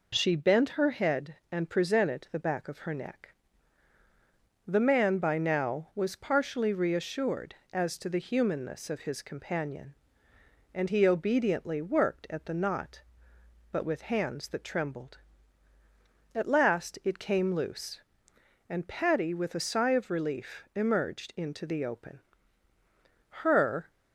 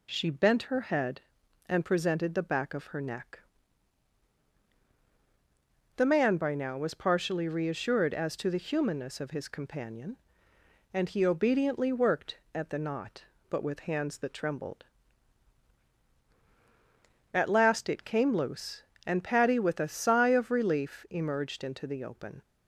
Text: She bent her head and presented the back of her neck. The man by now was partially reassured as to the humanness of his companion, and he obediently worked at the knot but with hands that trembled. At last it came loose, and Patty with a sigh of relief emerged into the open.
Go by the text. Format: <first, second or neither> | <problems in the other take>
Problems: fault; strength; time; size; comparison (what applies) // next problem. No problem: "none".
second | goes on to say "Her"; from 23.2 s on; 0.60 s long